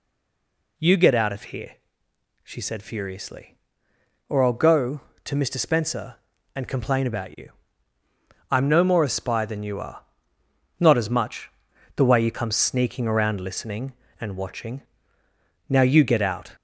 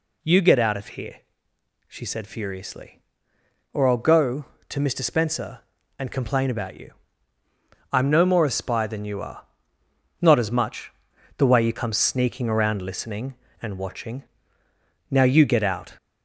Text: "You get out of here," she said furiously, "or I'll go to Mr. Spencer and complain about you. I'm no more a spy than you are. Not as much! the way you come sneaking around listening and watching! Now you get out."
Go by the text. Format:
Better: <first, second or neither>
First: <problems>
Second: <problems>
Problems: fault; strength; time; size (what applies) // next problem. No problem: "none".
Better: second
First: stays silent before the first word; slight; until 0.7 s; 0.7 s long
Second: none